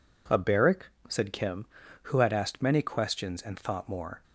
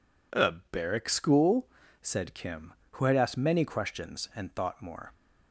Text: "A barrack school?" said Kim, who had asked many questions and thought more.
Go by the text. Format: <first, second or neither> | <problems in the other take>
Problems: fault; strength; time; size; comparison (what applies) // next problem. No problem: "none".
second | skips "school"; at 0.9 s